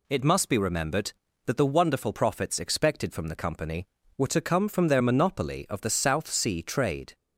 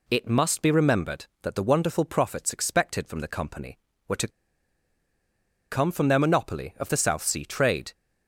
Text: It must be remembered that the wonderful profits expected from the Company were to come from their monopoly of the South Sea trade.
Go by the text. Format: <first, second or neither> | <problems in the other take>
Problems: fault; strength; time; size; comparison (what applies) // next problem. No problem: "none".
first | pauses between "to" and "come"; strong; at 4.2 s; 1.4 s long